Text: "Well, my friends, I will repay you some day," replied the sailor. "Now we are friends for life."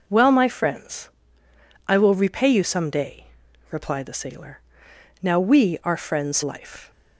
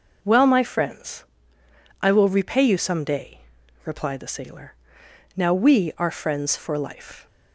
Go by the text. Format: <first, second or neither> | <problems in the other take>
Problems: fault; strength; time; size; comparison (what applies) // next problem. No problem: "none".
second | skips "for"; at 6.4 s